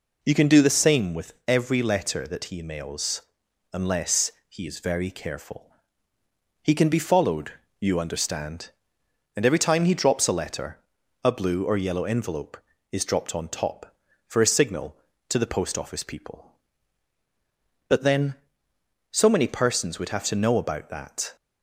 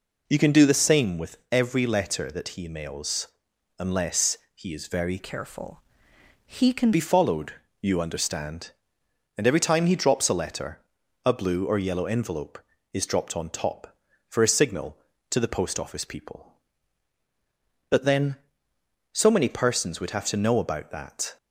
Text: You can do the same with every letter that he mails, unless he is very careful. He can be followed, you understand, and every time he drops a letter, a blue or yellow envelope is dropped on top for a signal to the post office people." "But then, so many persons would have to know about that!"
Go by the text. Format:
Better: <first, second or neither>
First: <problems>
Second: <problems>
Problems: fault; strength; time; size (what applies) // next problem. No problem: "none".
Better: first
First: pauses between "unless" and "he"; slight; at 4.3 s; 0.18 s long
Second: pauses between "unless" and "he"; slight; at 4.3 s; 0.18 s long // changes voice from "careful" to "can"; from 5.1 to 6.9 s; 1.8 s long